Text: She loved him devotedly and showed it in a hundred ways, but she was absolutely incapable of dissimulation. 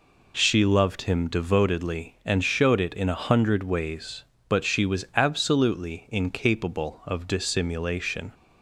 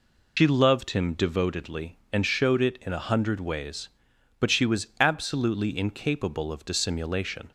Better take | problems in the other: first | loses the start of "She"; at 0.3 s; 100 ms

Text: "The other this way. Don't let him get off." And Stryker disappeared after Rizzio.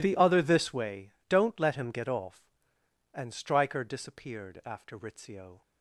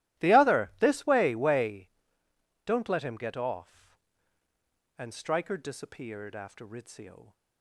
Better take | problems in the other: first | starts louder than the rest; strong; until 1.2 s; 15 dB // says "way" twice; at 1.3 s

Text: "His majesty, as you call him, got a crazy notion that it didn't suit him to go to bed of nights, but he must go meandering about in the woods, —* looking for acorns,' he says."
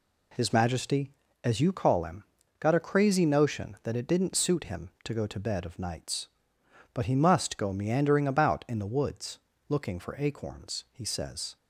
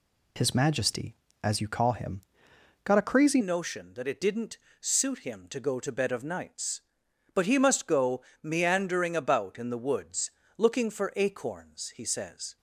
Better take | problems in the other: first | changes voice at "notion"; from 3.4 s on; 9.1 s long // pauses between "didn't" and "suit"; slight; at 4.5 s; 0.24 s long // pauses between "go" and "meandering"; slight; at 8.2 s; 0.22 s long

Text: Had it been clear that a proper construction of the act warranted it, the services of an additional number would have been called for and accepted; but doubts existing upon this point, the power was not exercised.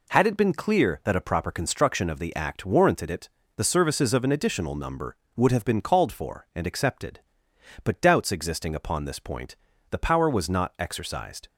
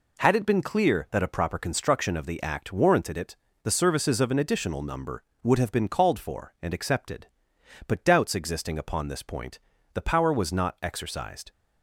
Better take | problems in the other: neither | none

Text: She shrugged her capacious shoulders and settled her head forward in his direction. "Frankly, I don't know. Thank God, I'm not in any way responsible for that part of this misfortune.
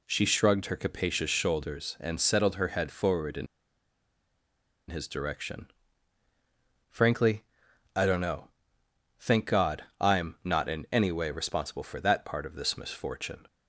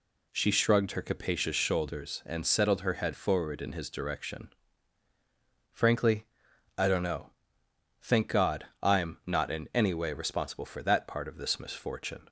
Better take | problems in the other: second | pauses between "in" and "his"; strong; at 3.4 s; 1.4 s long

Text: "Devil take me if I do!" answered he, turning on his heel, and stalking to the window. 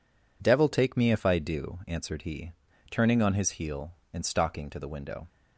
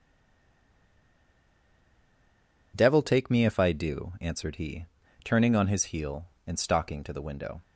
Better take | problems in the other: first | stays silent before the first word; strong; until 2.7 s; 2.7 s long

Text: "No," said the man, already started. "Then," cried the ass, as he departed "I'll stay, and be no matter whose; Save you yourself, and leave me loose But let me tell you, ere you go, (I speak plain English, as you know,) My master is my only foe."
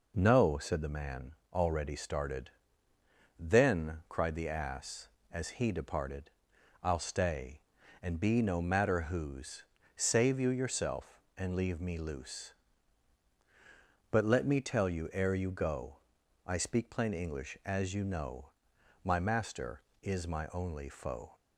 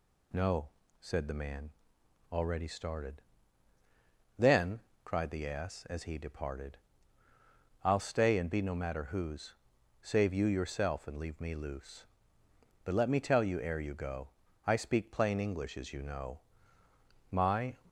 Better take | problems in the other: first | pauses between "departed" and "I'll"; at 6.7 s; 1.0 s long; noticeable in the first // stops before "master is my only foe"; at 17.8 s

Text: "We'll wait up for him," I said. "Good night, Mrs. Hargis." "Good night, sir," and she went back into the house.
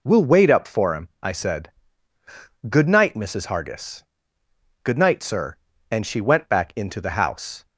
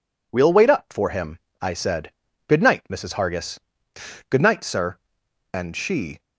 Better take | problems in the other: first | stops before "went back into the house"; at 6.1 s

